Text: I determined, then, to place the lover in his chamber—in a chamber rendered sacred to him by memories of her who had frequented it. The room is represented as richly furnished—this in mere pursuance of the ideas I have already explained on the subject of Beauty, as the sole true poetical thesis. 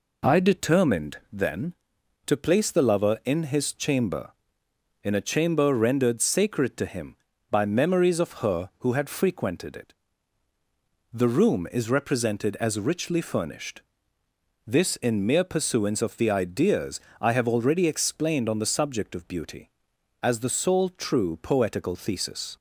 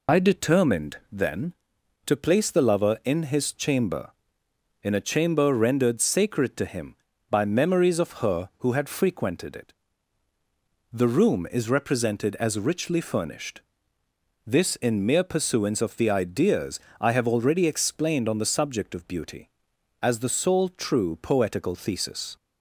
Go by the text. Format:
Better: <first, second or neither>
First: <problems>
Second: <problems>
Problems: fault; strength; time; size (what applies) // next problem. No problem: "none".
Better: first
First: pauses between "ideas" and "I"; slight; at 17.0 s; 0.18 s long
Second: loses the start of "I"; at 0.0 s; 60 ms // pauses between "ideas" and "I"; slight; at 16.8 s; 0.18 s long